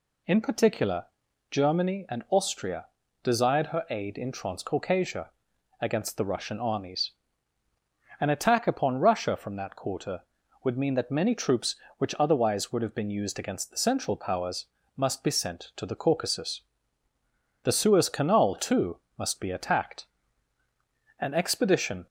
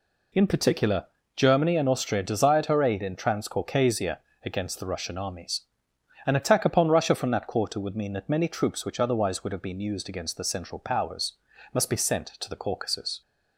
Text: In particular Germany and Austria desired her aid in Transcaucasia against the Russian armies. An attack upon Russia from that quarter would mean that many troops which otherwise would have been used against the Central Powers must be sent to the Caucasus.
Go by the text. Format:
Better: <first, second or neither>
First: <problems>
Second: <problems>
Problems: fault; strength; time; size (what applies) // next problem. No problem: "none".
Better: second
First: pauses between "particular" and "Germany"; at 1.0 s; 0.44 s long // pauses between "Austria" and "desired"; slight; at 2.8 s; 0.36 s long // pauses between "Transcaucasia" and "against"; noticeable; at 5.3 s; 0.50 s long // pauses between "Powers" and "must"; slight; at 14.6 s; 0.30 s long // goes on to say "The Suez Canal too must be attacked An expedition"; strong; from 17.6 s on; 4.4 s long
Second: pauses between "particular" and "Germany"; slight; at 1.0 s; 0.30 s long // pauses between "Transcaucasia" and "against"; slight; at 4.1 s; 0.26 s long // pauses between "Powers" and "must"; at 11.3 s; 0.40 s long